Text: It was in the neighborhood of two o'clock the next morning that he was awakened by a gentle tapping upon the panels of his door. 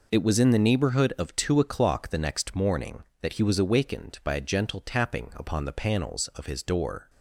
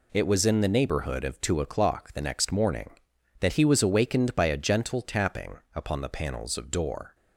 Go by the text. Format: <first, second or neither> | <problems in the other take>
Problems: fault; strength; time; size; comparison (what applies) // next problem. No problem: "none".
first | skips "his"; at 6.6 s